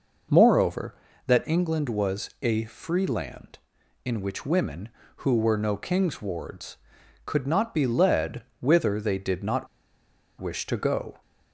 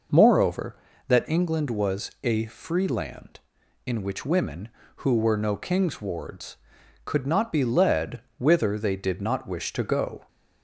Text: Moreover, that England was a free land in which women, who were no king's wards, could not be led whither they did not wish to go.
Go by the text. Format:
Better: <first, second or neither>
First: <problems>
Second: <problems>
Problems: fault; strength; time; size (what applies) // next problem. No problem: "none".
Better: second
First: pauses between "led" and "whither"; slight; at 8.4 s; 0.16 s long // pauses between "not" and "wish"; noticeable; at 9.6 s; 0.73 s long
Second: pauses between "led" and "whither"; slight; at 8.2 s; 0.16 s long